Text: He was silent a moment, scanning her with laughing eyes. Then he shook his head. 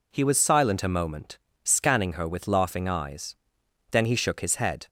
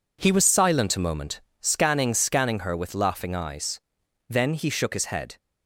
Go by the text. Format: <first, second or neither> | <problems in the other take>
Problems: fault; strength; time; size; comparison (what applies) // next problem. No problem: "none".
first | says "scanning" twice; at 2.1 s